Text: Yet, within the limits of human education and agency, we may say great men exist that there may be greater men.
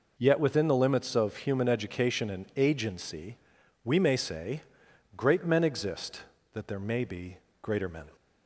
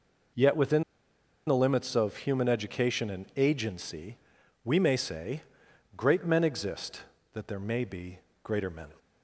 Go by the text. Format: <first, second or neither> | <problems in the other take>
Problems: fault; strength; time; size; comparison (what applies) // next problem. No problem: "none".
first | pauses between "within" and "the"; noticeable; at 0.8 s; 0.64 s long // pauses between "say" and "great"; noticeable; at 5.4 s; 0.54 s long; noticeable in the first // pauses between "be" and "greater"; slight; at 8.1 s; 0.24 s long; slight in the first